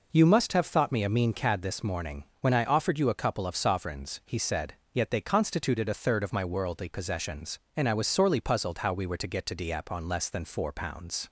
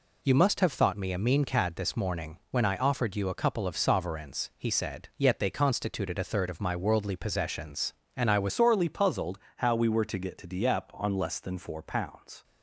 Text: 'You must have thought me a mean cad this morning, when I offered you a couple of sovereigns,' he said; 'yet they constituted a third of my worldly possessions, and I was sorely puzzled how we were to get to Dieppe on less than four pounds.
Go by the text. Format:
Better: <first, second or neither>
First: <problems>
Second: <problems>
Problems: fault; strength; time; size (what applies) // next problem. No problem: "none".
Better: first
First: none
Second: changes voice at "sorely"; from 8.5 s on; 3.9 s long // pauses between "puzzled" and "how"; slight; at 9.3 s; 0.18 s long